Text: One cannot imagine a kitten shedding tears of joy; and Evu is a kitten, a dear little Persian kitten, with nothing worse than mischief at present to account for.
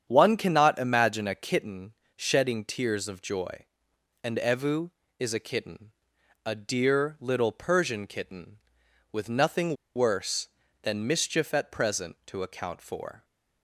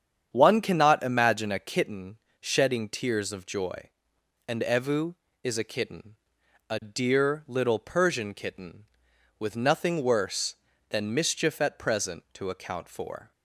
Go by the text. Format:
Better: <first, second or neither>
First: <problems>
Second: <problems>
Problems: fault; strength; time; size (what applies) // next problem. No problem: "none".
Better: second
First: starts louder than the rest; strong; until 1.0 s; 8 dB // pauses between "kitten" and "shedding"; slight; at 1.9 s; 0.24 s long // pauses between "nothing" and "worse"; slight; at 9.7 s; 0.20 s long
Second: starts louder than the rest; strong; until 1.3 s; 8 dB // pauses between "kitten" and "shedding"; slight; at 2.1 s; 0.24 s long